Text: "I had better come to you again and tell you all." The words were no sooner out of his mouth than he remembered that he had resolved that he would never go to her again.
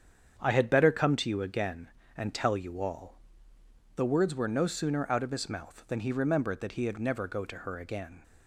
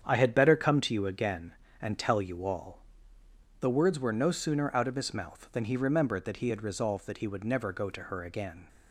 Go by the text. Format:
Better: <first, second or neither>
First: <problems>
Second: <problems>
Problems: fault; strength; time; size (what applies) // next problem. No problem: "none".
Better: second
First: starts louder than the rest; strong; until 1.3 s; 8 dB // skips "resolved that he would"; at 6.9 s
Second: starts louder than the rest; strong; until 1.0 s; 8 dB